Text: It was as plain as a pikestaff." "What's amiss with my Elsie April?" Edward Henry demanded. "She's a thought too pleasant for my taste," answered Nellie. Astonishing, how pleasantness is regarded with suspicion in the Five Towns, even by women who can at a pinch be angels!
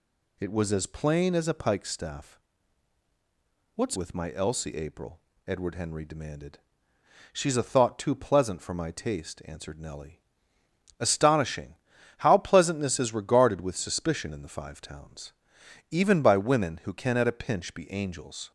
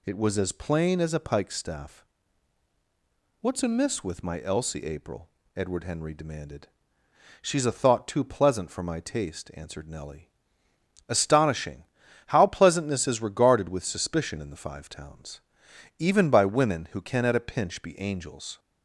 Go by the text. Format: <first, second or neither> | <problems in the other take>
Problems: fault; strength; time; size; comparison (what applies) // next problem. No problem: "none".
second | skips "amiss"; at 3.9 s